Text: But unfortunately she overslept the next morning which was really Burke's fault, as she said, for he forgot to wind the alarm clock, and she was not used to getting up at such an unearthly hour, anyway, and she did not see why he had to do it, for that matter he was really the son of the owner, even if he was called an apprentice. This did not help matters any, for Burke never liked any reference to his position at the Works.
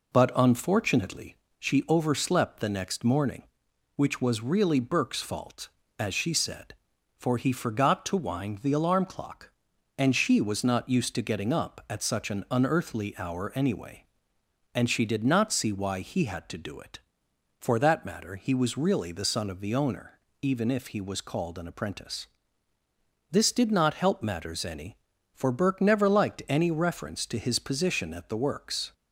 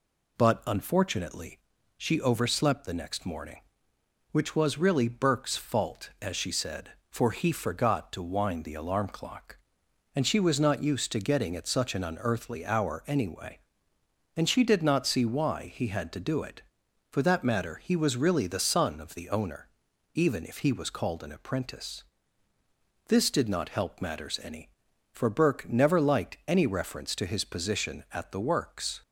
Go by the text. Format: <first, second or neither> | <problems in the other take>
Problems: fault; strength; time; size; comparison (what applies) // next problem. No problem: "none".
first | pauses between "unfortunately" and "she"; at 1.5 s; 0.38 s long; slight in the first // skips "up"; at 11.5 s